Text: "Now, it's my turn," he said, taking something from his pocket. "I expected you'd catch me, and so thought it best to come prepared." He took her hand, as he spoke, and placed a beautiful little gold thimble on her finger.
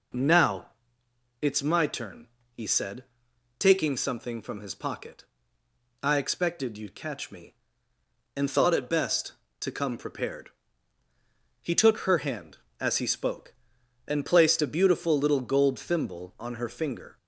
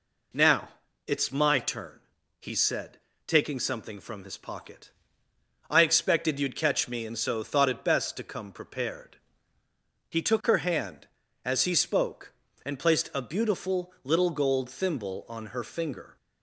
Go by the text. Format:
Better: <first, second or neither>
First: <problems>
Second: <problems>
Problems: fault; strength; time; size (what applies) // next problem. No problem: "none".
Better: second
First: skips "so"; at 8.4 s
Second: none